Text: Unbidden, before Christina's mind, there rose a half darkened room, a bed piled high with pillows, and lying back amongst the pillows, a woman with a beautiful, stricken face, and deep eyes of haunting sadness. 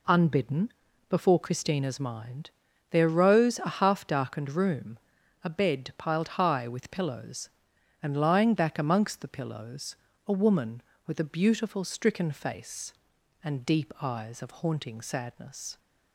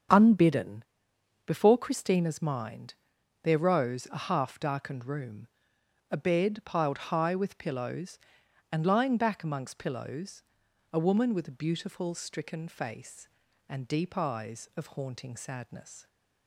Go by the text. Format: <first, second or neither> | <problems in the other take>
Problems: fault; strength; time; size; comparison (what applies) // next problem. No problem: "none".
first | starts louder than the rest; strong; until 1.7 s; 7.5 dB // skips "the"; at 9.7 s